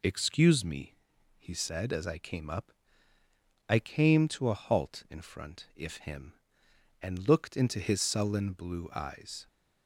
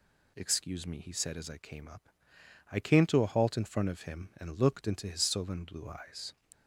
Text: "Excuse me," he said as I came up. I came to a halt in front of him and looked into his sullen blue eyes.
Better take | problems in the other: second | says "if" for "of"; at 5.7 s

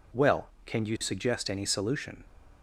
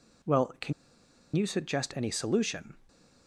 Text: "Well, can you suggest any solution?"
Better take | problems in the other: first | pauses between "can" and "you"; noticeable; at 0.7 s; 0.63 s long // stays silent after the last word; slight; from 2.7 s on; 0.5 s long

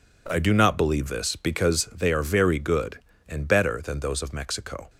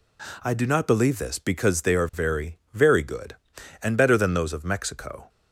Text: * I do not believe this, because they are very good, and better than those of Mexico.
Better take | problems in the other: first | says "very" twice; at 2.7 s

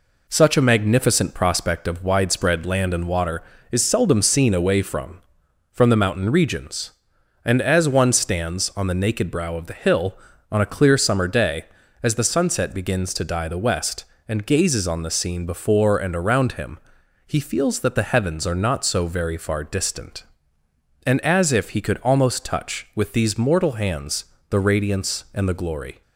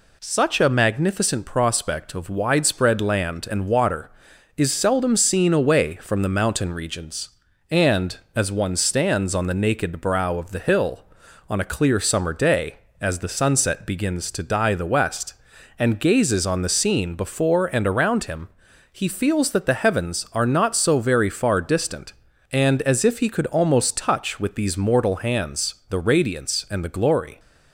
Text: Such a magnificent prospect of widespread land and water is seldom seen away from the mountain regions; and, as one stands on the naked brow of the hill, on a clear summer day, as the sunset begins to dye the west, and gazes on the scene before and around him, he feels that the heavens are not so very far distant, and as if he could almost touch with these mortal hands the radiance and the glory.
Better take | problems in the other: second | says "from" twice; at 5.7 s // pauses between "hands" and "the"; slight; at 24.2 s; 0.24 s long

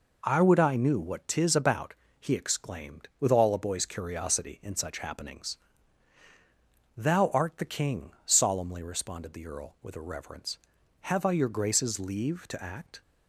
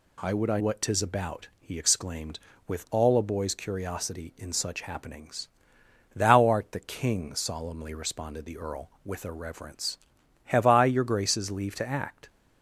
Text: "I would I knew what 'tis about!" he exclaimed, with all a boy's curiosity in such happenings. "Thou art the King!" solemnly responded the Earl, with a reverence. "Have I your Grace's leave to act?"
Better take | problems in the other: first | skips "knew"; at 0.5 s

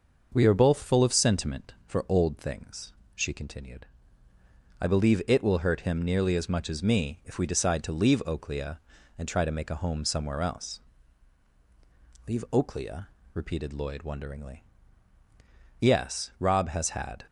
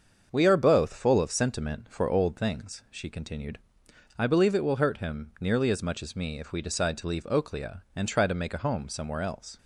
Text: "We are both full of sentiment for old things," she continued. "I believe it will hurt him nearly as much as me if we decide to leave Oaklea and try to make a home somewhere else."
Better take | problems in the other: second | starts louder than the rest; until 1.3 s; 6 dB; also in the second // goes on to say "Leave Oaklea repeated Lloyd wonderingly Yes Rob has had"; strong; from 12.2 s on; 4.9 s long

